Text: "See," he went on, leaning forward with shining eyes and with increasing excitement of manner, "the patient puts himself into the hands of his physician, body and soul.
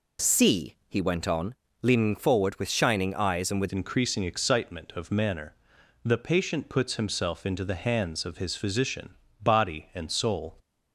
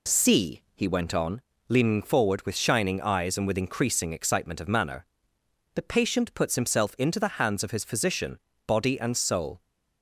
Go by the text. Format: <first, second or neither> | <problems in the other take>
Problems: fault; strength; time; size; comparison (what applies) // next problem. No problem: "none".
second | changes voice at "increasing"; from 3.7 s on; 6.8 s long